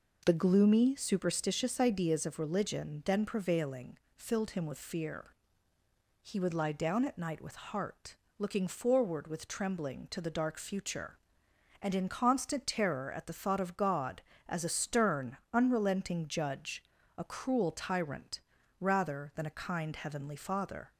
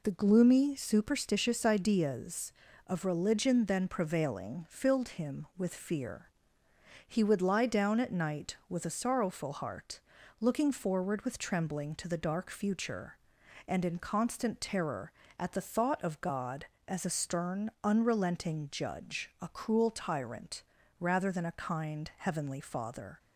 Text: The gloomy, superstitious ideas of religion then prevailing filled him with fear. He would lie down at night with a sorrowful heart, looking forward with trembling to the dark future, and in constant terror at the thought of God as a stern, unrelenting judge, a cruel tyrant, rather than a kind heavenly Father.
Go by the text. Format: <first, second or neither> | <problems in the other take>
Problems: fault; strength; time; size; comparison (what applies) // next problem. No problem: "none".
second | pauses between "prevailing" and "filled"; slight; at 3.9 s; 0.18 s long // skips "a sorrowful"; at 7.5 s